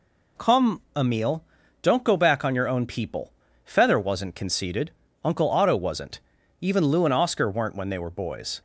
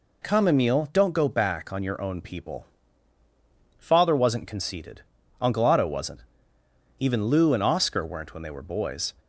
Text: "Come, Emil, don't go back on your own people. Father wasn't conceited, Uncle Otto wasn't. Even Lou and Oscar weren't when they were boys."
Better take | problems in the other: second | says "Feather" for "Father"; at 3.6 s

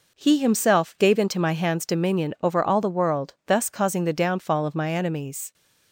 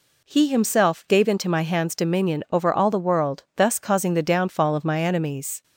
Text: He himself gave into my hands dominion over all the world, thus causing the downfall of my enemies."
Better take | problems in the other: second | gets quieter; throughout; 6.5 dB

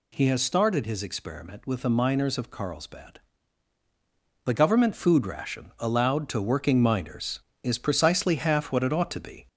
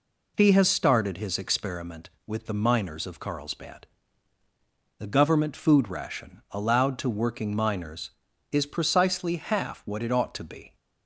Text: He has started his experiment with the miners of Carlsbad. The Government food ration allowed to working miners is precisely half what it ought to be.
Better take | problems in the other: second | gets louder; slight; throughout; 2.5 dB

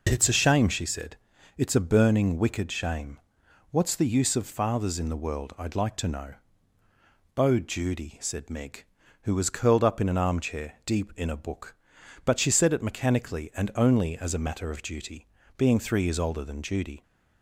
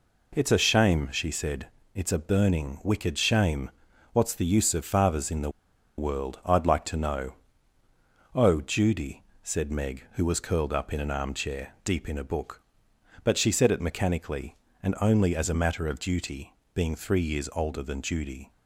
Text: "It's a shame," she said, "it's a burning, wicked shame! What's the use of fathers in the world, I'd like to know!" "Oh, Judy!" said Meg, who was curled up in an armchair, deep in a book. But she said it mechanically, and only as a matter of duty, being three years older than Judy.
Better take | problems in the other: first | pauses between "the" and "world"; noticeable; at 5.4 s; 0.48 s long

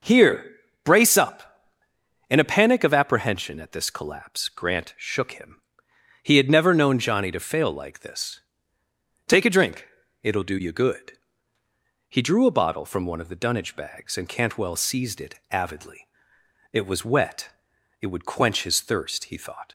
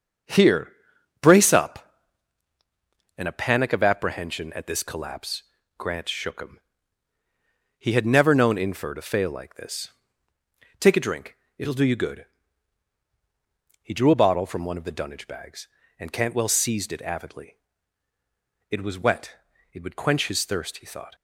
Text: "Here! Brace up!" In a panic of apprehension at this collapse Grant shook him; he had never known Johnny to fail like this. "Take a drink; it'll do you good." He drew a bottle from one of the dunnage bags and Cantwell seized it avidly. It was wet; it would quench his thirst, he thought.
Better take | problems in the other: first | starts louder than the rest; until 1.7 s; 7 dB // pauses between "collapse" and "Grant"; slight; at 5.4 s; 0.36 s long // says "Infer" for "Johnny"; at 8.5 s

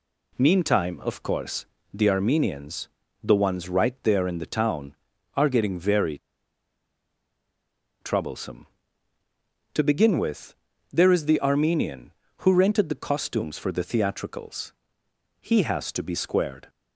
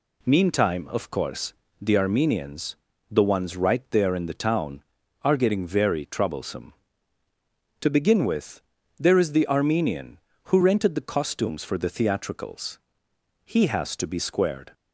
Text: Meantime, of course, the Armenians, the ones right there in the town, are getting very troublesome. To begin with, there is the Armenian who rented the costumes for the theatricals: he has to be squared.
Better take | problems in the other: second | pauses between "very" and "troublesome"; strong; at 6.1 s; 1.8 s long

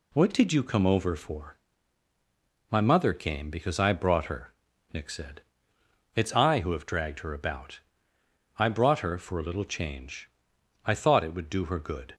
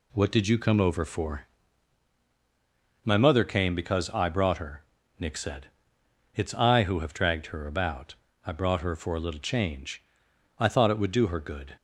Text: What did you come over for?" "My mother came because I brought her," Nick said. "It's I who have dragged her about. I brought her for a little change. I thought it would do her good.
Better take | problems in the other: neither | none

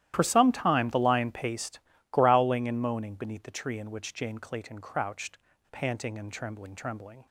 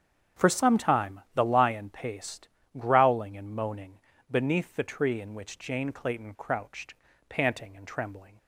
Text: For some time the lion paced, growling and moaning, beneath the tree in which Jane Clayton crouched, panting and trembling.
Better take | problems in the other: second | starts louder than the rest; strong; until 1.1 s; 13 dB; strong in the second // says "trembling" twice; at 6.7 s

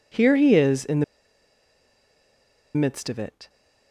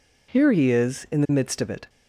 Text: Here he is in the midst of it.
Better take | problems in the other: second | pauses between "the" and "midst"; strong; at 1.0 s; 1.7 s long

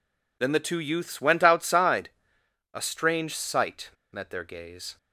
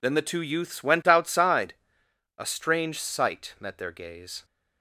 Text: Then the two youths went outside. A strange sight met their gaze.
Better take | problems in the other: second | pauses between "sight" and "met"; slight; at 3.9 s; 0.22 s long

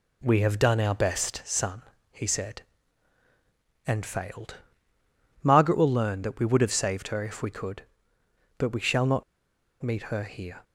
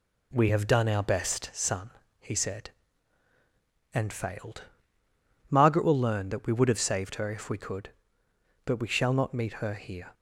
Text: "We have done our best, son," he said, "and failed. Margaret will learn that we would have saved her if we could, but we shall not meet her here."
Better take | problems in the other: second | pauses between "not" and "meet"; noticeable; at 9.2 s; 0.59 s long

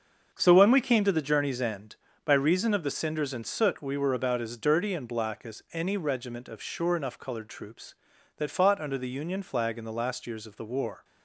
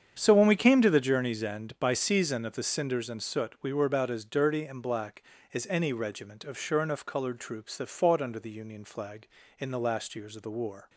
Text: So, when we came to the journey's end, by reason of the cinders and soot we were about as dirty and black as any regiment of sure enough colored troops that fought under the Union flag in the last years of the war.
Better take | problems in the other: first | starts louder than the rest; strong; until 1.2 s; 8 dB; also in the first // says "season" for "reason"; at 1.9 s

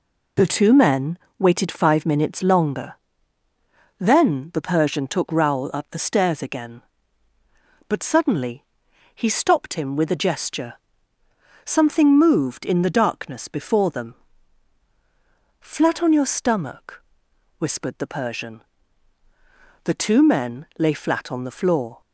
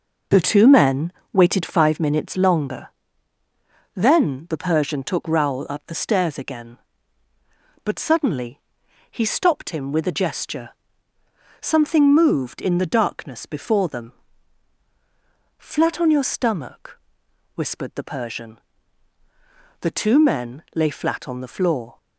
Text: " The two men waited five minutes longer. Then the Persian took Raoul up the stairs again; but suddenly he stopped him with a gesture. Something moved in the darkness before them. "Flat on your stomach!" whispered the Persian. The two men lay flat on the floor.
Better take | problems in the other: first | starts louder than the rest; noticeable; until 2.0 s; 5.5 dB // pauses between "men" and "waited"; slight; at 1.1 s; 0.22 s long; slight in the first // pauses between "suddenly" and "he"; noticeable; at 8.5 s; 0.52 s long; noticeable in the first

